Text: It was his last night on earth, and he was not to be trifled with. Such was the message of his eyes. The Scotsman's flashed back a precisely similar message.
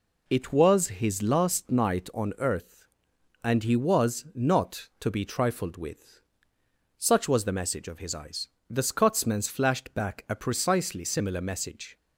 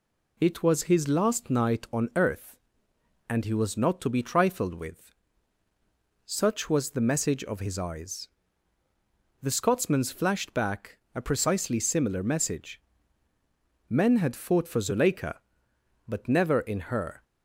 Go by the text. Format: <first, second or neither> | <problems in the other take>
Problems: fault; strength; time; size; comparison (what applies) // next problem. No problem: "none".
first | pauses between "back" and "a"; slight; at 10.9 s; 0.16 s long // goes on to say "Men had fought for Zuleika but never in her"; strong; from 13.8 s on; 3.3 s long